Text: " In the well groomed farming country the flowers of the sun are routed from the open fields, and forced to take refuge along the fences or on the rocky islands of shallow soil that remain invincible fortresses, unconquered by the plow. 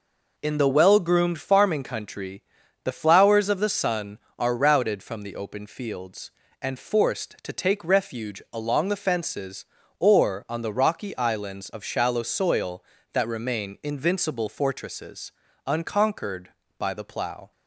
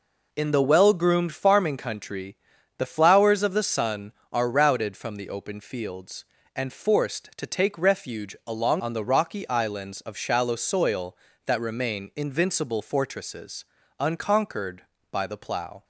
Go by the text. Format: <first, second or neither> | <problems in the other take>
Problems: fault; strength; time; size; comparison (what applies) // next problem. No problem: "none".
first | pauses between "country" and "the"; at 2.3 s; 0.40 s long; also in the first // skips "the fences or"; at 8.7 s